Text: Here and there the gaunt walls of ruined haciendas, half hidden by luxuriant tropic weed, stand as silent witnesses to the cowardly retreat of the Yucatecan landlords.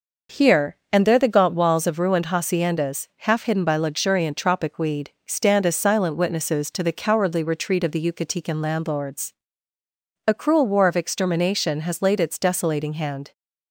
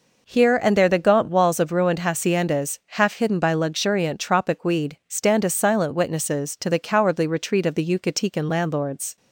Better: second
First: goes on to say "A cruel war of extermination has laid its desolating hand"; strong; from 10.2 s on; 3.0 s long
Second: none

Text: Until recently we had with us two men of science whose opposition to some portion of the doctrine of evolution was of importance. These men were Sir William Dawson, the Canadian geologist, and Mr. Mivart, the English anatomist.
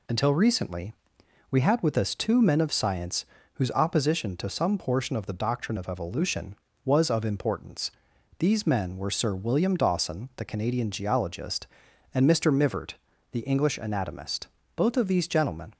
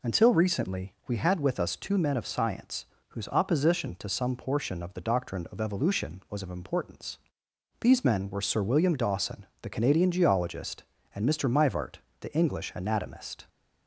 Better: second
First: pauses between "recently" and "we"; noticeable; at 0.9 s; 0.58 s long // pauses between "science" and "whose"; slight; at 3.2 s; 0.30 s long // goes on to say "Both of these gentlemen"; noticeable; from 14.7 s on; 0.98 s long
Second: pauses between "science" and "whose"; slight; at 2.8 s; 0.22 s long

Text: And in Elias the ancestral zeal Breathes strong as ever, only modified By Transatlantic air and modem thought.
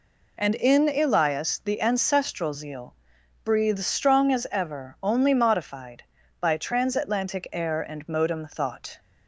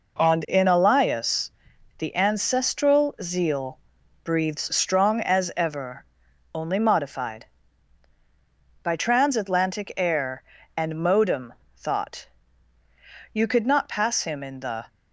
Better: first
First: pauses between "zeal" and "Breathes"; noticeable; at 2.9 s; 0.48 s long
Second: pauses between "Elias" and "the"; noticeable; at 1.4 s; 0.46 s long // pauses between "zeal" and "Breathes"; at 3.7 s; 0.42 s long // pauses between "modem" and "thought"; slight; at 11.5 s; 0.20 s long // goes on to say "You could not pass him in the"; from 13.3 s on; 1.5 s long

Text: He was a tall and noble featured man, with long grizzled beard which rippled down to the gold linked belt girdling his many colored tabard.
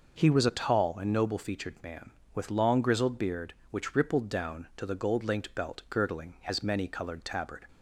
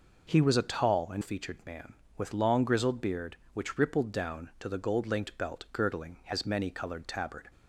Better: first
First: none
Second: skips "noble"; at 1.2 s

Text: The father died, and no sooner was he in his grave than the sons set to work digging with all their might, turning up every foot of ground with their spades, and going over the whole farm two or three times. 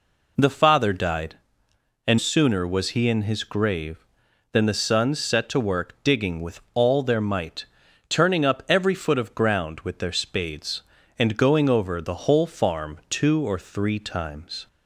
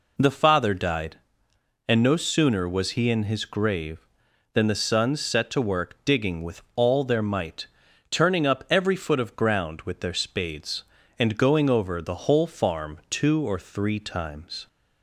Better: second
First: skips "no"; at 2.1 s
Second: none

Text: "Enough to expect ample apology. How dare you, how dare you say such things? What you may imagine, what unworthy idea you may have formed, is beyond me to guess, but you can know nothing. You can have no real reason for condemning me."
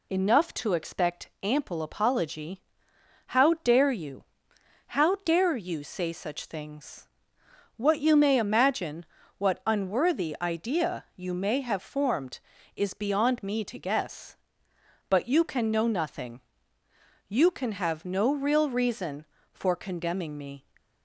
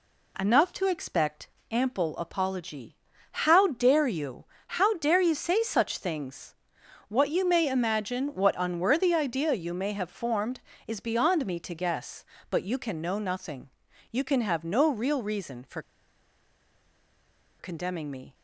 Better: first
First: none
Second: pauses between "expect" and "ample"; slight; at 1.4 s; 0.22 s long // pauses between "for" and "condemning"; strong; at 15.7 s; 1.7 s long

